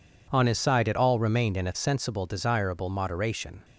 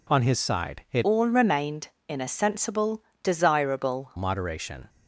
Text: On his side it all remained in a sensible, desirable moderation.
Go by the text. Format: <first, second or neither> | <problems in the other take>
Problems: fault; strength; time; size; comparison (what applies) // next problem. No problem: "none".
first | changes voice from "all" to "desirable"; from 1.0 to 4.1 s; 3.1 s long